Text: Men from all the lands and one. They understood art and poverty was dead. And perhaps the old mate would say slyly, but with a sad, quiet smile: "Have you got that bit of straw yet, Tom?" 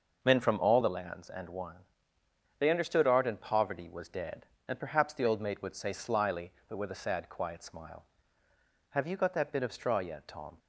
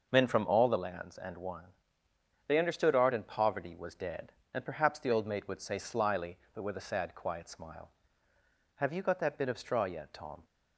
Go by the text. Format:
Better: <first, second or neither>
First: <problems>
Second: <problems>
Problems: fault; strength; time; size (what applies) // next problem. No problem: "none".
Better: neither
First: starts louder than the rest; noticeable; until 1.2 s; 6 dB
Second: starts louder than the rest; noticeable; until 1.1 s; 6 dB